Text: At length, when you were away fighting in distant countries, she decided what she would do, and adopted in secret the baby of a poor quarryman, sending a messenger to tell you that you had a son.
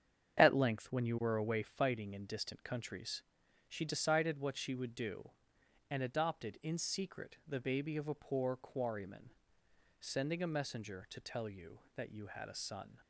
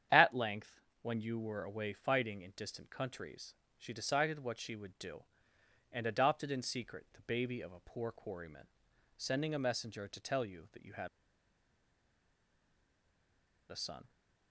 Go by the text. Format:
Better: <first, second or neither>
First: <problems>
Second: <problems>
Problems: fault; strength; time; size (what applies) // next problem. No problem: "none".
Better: first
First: starts louder than the rest; strong; until 1.4 s; 8.5 dB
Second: starts louder than the rest; strong; until 1.3 s; 9 dB // pauses between "had" and "a"; strong; at 11.0 s; 2.6 s long